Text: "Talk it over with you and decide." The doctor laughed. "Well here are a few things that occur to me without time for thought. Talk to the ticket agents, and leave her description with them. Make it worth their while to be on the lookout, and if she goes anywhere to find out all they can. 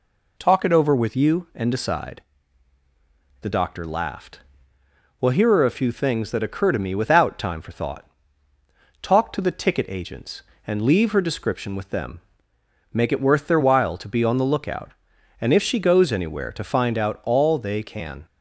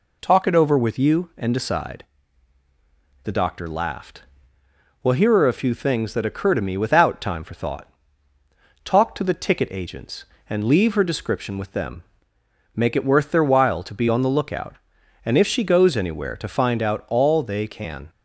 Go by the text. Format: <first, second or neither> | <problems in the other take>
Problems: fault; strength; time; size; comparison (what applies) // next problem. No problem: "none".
neither | none